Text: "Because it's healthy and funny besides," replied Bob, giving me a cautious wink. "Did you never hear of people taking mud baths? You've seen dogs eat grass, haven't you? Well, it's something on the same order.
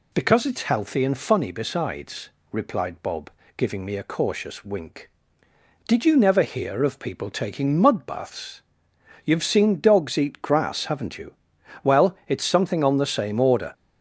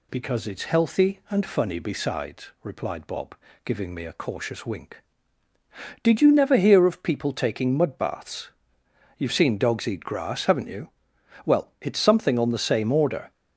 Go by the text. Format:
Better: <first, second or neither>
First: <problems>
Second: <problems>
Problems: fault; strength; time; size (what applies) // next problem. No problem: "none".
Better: neither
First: none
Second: none